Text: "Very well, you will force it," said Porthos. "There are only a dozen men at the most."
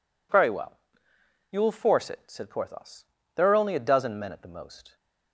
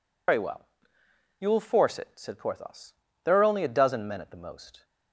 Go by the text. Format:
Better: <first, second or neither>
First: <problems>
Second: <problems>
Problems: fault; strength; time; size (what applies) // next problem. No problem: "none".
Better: first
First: none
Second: loses the start of "Very"; at 0.2 s; 85 ms